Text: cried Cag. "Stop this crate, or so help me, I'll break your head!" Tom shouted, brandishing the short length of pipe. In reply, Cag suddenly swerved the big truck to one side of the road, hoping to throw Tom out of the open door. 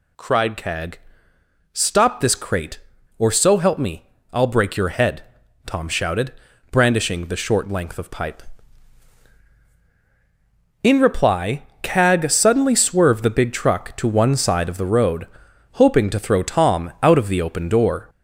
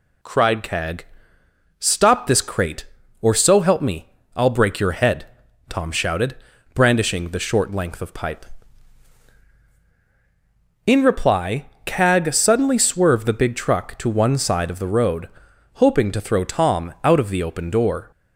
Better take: second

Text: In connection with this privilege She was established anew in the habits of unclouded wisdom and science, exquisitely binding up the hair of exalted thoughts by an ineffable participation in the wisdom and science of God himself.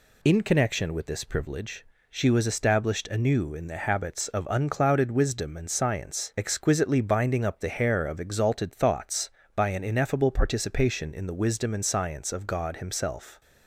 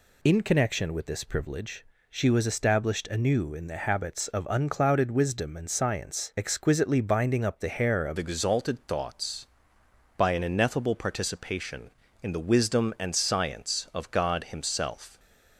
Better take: first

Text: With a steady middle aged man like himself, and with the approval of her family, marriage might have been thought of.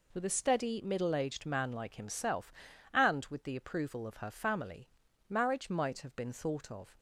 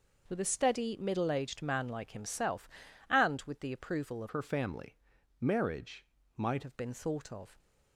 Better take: first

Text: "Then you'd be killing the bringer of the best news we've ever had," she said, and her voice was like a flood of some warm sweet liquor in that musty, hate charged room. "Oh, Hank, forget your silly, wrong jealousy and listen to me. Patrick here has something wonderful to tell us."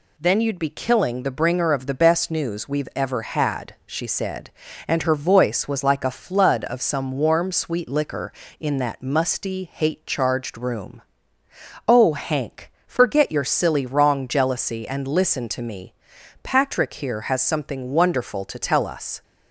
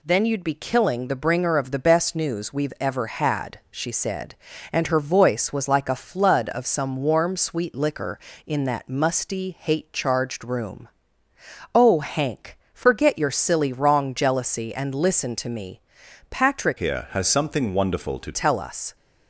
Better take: first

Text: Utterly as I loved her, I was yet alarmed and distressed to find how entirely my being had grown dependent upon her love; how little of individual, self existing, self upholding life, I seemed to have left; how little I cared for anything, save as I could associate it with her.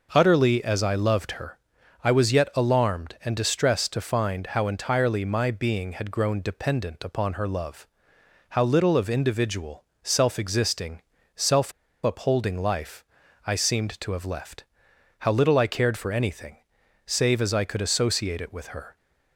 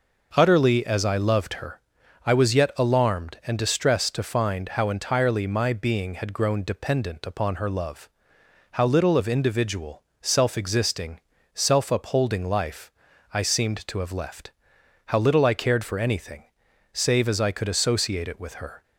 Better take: second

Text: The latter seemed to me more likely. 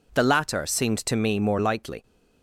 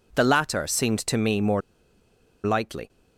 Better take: first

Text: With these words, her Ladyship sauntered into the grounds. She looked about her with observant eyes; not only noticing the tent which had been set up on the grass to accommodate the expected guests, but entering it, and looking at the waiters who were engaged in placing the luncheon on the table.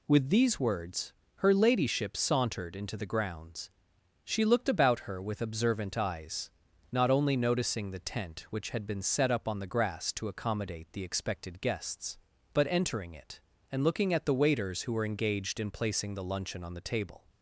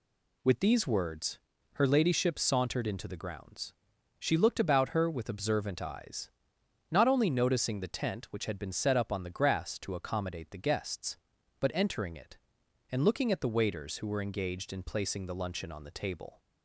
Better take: first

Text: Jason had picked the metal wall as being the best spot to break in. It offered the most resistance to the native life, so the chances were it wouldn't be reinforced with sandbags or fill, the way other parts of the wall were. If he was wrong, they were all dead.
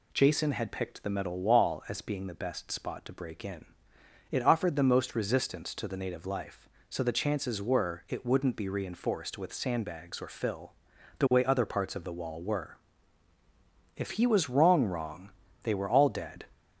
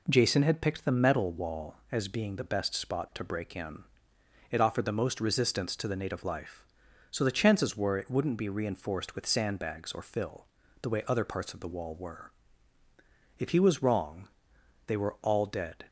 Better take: second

